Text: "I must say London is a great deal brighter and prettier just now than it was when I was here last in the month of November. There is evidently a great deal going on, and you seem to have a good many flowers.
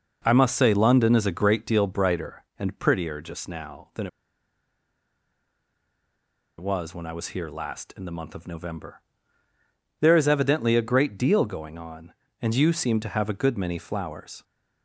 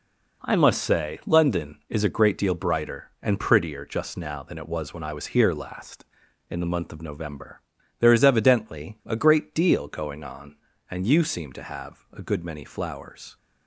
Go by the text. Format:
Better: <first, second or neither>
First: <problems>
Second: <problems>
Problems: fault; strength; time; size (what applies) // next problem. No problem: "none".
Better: second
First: pauses between "than" and "it"; strong; at 4.0 s; 2.5 s long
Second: none